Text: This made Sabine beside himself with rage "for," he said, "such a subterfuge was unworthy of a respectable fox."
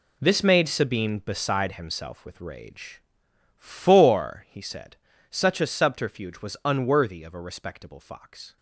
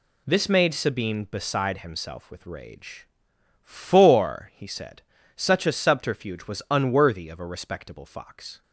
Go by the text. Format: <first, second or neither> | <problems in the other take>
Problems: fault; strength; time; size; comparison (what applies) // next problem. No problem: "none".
second | gets quieter; strong; throughout; 11.5 dB